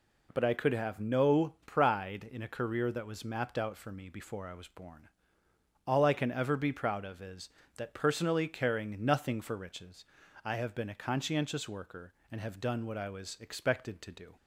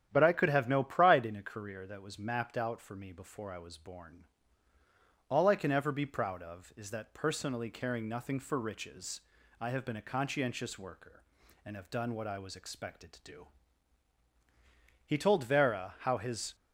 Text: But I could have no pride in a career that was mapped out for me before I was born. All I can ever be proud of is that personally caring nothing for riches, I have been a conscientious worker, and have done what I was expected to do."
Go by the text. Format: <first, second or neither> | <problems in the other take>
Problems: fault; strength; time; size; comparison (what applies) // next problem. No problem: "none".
first | starts louder than the rest; strong; until 1.1 s; 10 dB // goes on to say "He told Vera how his"; from 15.0 s on; 1.5 s long